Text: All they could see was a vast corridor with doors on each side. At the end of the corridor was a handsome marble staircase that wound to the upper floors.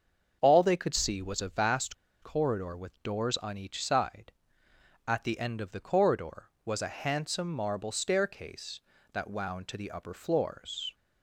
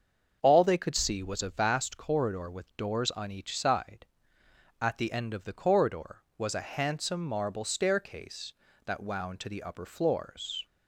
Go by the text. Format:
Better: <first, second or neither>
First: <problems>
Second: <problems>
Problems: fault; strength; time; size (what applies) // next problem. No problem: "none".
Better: second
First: starts louder than the rest; until 1.4 s; 6.5 dB // pauses between "vast" and "corridor"; slight; at 1.9 s; 0.29 s long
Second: starts louder than the rest; until 1.4 s; 6.5 dB